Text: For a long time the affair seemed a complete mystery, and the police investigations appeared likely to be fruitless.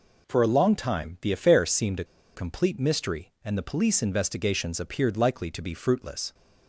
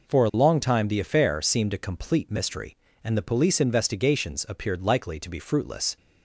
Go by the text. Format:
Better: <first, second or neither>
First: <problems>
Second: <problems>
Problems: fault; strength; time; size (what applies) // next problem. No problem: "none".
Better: second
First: pauses between "a" and "complete"; slight; at 2.0 s; 0.30 s long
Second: none